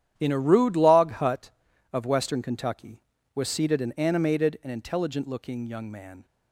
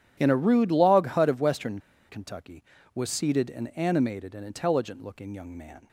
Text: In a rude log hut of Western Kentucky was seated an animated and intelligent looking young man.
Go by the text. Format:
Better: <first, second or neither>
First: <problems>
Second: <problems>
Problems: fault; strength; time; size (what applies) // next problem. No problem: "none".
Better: first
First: starts louder than the rest; strong; until 1.1 s; 10.5 dB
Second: starts louder than the rest; strong; until 1.1 s; 10 dB // pauses between "Western" and "Kentucky"; slight; at 1.7 s; 0.30 s long